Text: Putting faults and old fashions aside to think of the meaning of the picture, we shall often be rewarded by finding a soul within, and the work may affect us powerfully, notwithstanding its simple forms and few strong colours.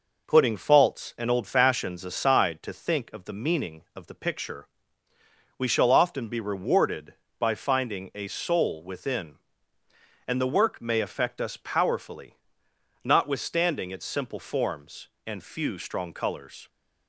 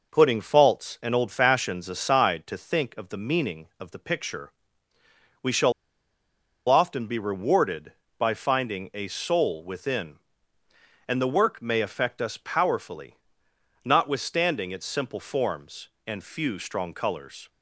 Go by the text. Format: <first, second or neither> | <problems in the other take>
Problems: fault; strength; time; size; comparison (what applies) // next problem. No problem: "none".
first | pauses between "shall" and "often"; noticeable; at 5.7 s; 0.96 s long